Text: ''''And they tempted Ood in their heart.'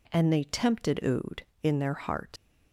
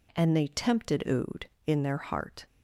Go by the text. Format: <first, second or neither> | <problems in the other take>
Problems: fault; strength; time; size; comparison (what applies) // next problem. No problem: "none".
second | leaves "heart" unfinished; at 2.3 s; 60 ms